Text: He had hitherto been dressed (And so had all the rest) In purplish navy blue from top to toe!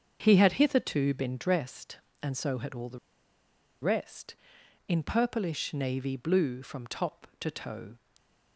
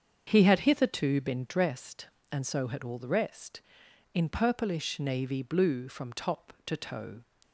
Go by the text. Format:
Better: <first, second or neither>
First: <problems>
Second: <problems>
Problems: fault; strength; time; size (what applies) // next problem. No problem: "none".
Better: second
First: starts louder than the rest; until 1.2 s; 7 dB // pauses between "the" and "rest"; noticeable; at 2.9 s; 0.83 s long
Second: starts louder than the rest; until 1.2 s; 7 dB